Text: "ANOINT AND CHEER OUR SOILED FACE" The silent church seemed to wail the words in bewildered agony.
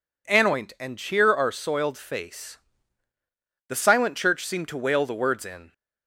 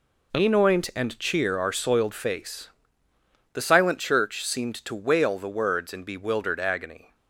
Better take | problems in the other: second | pauses between "FACE" and "The"; at 2.5 s; 1.1 s long; noticeable in the second // stops before "bewildered agony"; at 5.7 s

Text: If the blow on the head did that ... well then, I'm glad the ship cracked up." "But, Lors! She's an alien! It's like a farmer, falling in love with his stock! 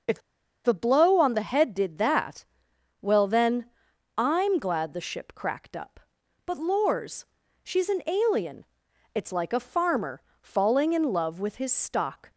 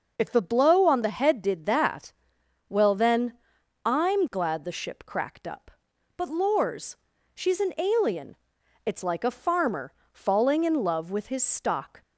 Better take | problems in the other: second | pauses between "If" and "the"; at 0.2 s; 0.43 s long

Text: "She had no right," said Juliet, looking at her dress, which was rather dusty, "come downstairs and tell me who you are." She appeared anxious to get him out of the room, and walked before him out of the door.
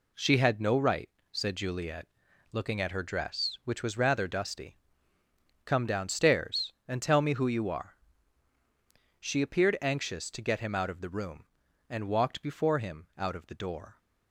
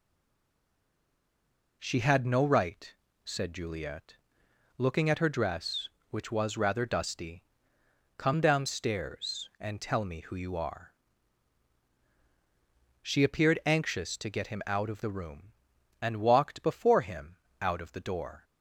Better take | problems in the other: first | stays silent before the first word; noticeable; until 1.8 s; 1.8 s long // pauses between "him" and "out"; slight; at 17.3 s; 0.24 s long

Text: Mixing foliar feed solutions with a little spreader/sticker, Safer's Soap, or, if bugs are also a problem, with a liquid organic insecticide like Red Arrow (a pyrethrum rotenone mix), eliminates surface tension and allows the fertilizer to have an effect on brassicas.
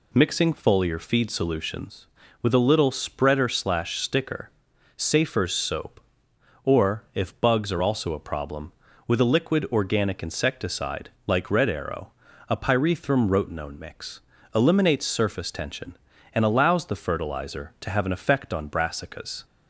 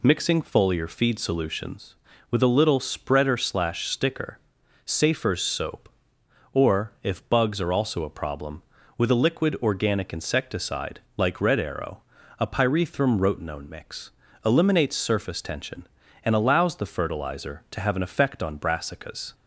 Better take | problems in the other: neither | pauses between "insecticide" and "like"; slight; the same in both

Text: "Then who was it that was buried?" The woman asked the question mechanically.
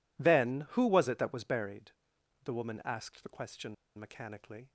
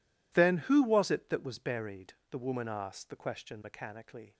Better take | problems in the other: second | pauses between "question" and "mechanically"; slight; at 3.7 s; 0.23 s long

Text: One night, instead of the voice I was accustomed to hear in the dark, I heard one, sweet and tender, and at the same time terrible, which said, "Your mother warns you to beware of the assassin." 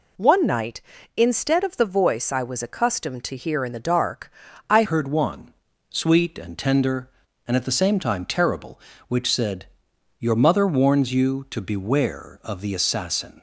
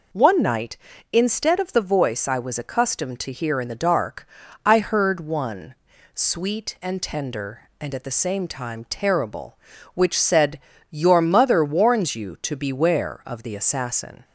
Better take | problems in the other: second | changes voice at "heard"; from 4.8 s on; 8.6 s long

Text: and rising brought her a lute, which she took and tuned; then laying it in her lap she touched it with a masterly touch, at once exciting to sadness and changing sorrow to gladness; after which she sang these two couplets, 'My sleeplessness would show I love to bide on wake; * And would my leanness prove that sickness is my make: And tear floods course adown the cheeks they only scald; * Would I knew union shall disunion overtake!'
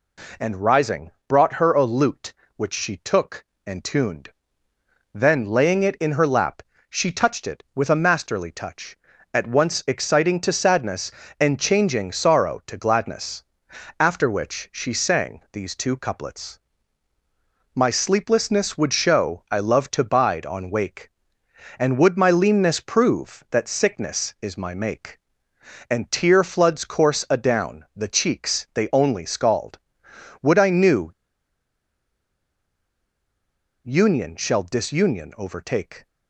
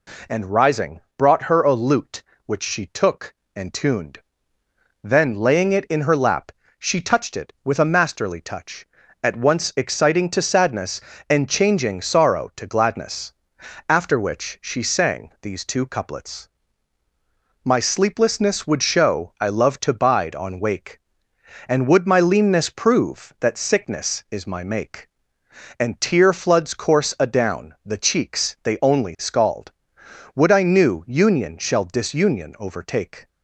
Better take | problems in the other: second | pauses between "rising" and "brought"; slight; at 1.1 s; 0.16 s long; slight in the second // pauses between "lap" and "she"; slight; at 6.6 s; 0.26 s long; slight in the second // pauses between "knew" and "union"; strong; at 31.1 s; 2.7 s long

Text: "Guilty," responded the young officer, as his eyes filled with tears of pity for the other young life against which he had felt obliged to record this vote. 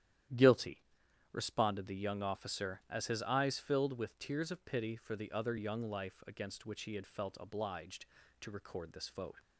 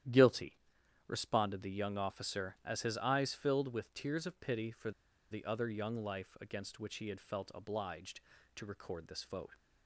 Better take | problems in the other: first | starts louder than the rest; strong; until 1.5 s; 11 dB; strong in the first // pauses between "for" and "the"; at 4.9 s; 0.40 s long

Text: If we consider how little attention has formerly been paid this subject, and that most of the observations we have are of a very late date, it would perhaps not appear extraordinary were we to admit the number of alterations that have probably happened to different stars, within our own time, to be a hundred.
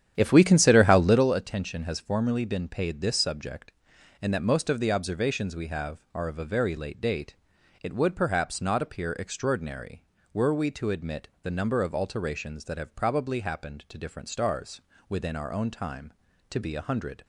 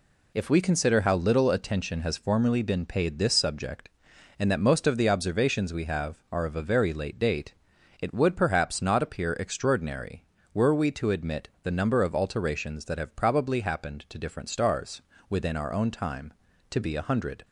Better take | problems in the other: second | starts louder than the rest; strong; until 1.3 s; 9.5 dB // pauses between "admit" and "the"; slight; at 11.2 s; 0.16 s long; slight in the second

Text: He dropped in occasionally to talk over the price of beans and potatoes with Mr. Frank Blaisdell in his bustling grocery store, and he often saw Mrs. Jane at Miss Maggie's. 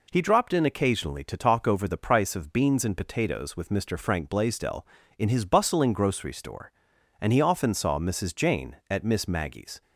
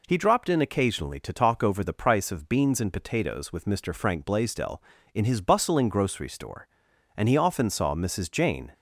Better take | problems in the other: first | stops before "at Miss Maggie's"; at 8.7 s

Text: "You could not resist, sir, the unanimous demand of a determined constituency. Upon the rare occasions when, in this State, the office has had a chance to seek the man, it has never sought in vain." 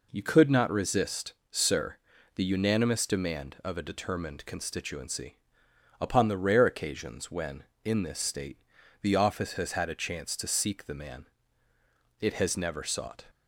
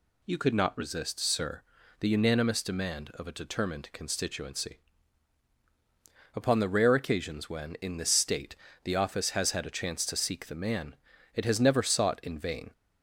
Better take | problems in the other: second | stops before "in vain"; at 13.2 s

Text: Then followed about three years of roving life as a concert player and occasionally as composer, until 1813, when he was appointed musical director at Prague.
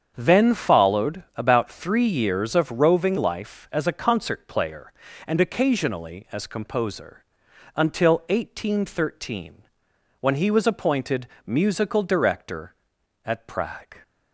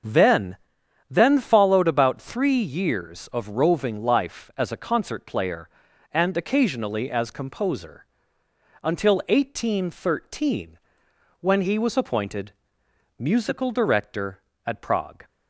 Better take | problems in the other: first | starts louder than the rest; until 1.5 s; 7 dB; strong in the first // says "Then" twice; at 1.1 s // pauses between "appointed" and "musical"; noticeable; at 12.5 s; 0.66 s long; slight in the first

